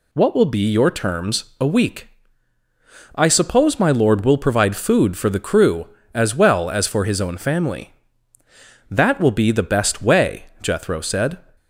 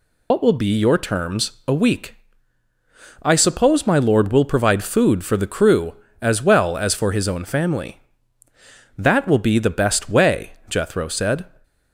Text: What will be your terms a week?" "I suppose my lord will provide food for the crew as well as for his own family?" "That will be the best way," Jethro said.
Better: first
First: pauses between "terms" and "a"; slight; at 1.4 s; 0.16 s long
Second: loses the start of "What"; at 0.3 s; 95 ms // pauses between "terms" and "a"; slight; at 1.5 s; 0.16 s long

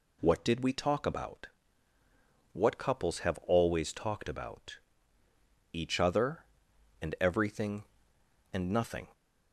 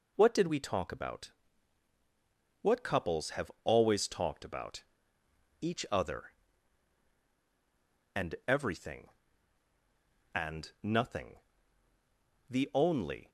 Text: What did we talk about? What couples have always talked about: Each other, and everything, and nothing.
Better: first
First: none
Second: goes on to say "The only"; noticeable; from 12.4 s on; 0.82 s long

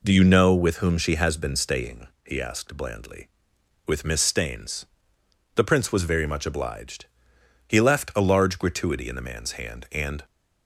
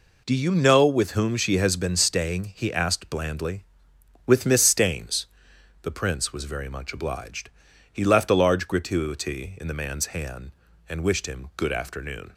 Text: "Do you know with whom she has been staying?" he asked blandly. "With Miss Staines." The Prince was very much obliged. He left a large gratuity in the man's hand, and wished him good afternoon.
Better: second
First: stops before "wished him good afternoon"; at 10.2 s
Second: none

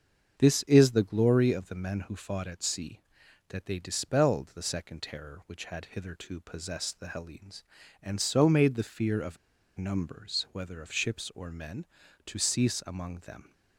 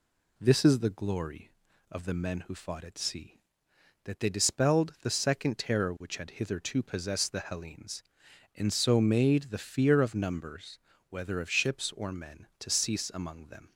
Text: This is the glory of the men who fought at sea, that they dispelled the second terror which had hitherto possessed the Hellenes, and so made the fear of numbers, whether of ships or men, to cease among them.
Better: second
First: starts louder than the rest; until 1.3 s; 7 dB // pauses between "of" and "numbers"; at 9.3 s; 0.41 s long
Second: none

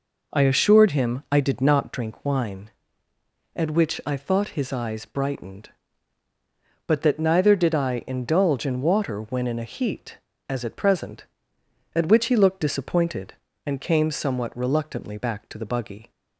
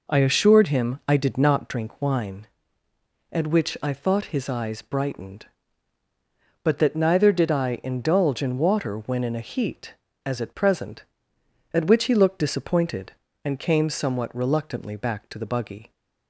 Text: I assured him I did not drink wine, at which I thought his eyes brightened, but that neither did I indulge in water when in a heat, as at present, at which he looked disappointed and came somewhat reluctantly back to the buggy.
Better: neither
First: none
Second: none

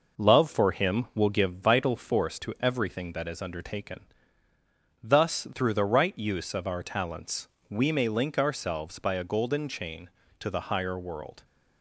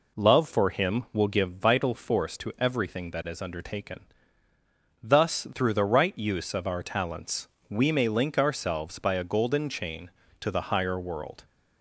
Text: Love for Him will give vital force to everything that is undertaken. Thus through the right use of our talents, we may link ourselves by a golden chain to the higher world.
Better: second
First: gets quieter; throughout; 3.5 dB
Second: none

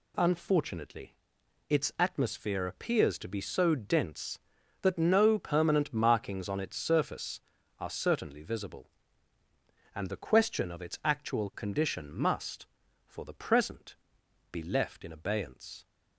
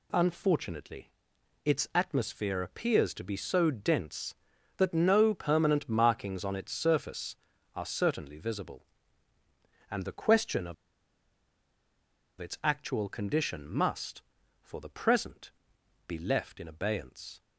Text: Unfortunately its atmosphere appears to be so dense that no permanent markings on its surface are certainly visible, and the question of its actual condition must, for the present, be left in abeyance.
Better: first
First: pauses between "Unfortunately" and "its"; noticeable; at 1.1 s; 0.54 s long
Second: pauses between "Unfortunately" and "its"; noticeable; at 1.0 s; 0.54 s long // pauses between "of" and "its"; strong; at 10.7 s; 1.6 s long

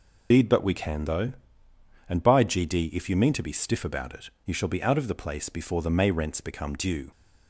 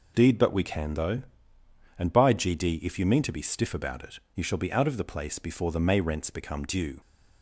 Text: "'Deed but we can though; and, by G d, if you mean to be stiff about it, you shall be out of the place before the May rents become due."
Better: second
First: loses the start of "Deed"; at 0.3 s; 55 ms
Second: none

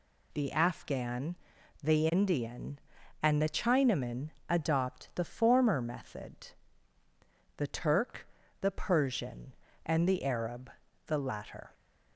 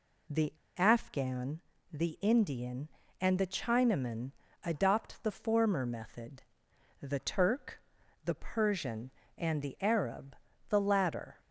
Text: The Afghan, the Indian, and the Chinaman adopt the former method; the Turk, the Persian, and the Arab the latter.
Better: first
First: pauses between "Chinaman" and "adopt"; slight; at 4.2 s; 0.20 s long // pauses between "Arab" and "the"; slight; at 10.7 s; 0.34 s long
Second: pauses between "The" and "Afghan"; slight; at 0.5 s; 0.24 s long // pauses between "Chinaman" and "adopt"; slight; at 4.2 s; 0.32 s long // pauses between "Arab" and "the"; slight; at 10.3 s; 0.34 s long

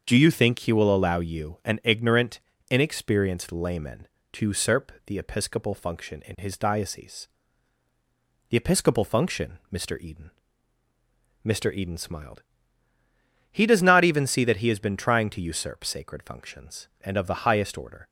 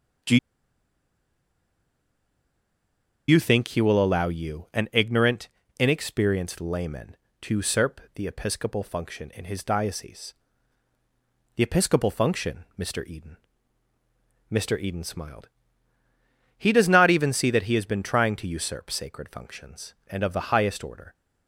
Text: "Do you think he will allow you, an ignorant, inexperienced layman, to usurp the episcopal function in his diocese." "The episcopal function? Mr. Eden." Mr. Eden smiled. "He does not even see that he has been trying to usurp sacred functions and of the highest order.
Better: first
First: starts louder than the rest; until 1.0 s; 6.5 dB // pauses between "usurp" and "the"; slight; at 4.9 s; 0.16 s long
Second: starts louder than the rest; until 4.1 s; 6.5 dB // pauses between "Do" and "you"; strong; at 0.3 s; 2.9 s long // pauses between "usurp" and "the"; slight; at 7.9 s; 0.16 s long

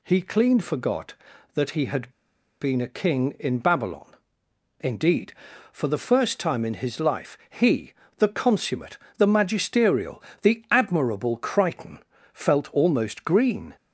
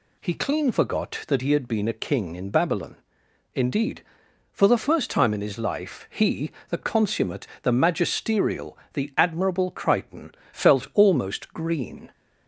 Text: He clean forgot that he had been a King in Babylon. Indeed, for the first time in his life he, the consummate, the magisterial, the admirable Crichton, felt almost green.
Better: second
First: pauses between "had" and "been"; noticeable; at 2.1 s; 0.51 s long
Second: none

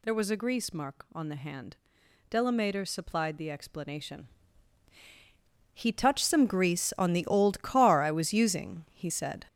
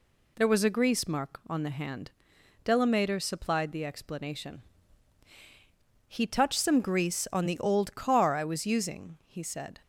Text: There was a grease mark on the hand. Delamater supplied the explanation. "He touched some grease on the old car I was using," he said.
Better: second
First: gets louder; strong; throughout; 7.5 dB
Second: none

